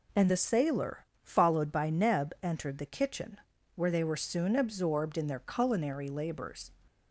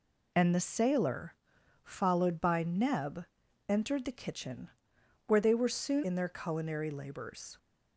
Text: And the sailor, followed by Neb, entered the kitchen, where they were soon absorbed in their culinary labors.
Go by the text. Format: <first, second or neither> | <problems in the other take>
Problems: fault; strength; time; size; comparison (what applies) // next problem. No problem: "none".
first | skips "absorbed"; at 6.0 s